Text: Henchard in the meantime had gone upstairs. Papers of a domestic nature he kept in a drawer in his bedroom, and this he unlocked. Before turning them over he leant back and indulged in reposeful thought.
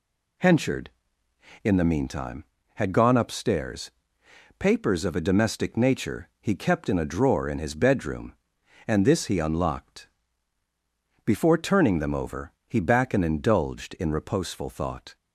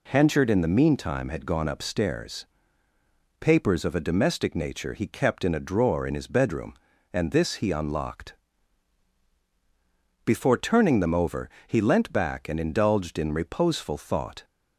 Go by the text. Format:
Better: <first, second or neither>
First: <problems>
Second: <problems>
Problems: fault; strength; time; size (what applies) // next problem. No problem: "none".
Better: second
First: pauses between "over" and "he"; slight; at 12.5 s; 0.16 s long // skips "leant"; at 12.7 s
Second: pauses between "over" and "he"; slight; at 11.4 s; 0.18 s long